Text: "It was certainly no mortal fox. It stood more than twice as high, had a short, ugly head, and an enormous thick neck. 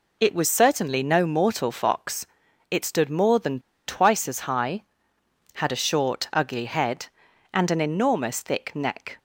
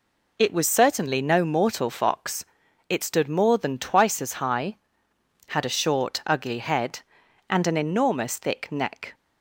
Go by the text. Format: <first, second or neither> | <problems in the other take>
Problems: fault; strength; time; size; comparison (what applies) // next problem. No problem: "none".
second | pauses between "than" and "twice"; slight; at 3.5 s; 0.28 s long